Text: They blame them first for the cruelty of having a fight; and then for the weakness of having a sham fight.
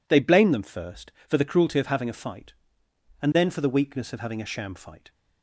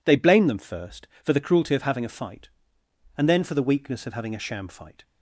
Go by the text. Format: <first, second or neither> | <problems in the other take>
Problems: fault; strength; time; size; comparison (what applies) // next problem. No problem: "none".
neither | none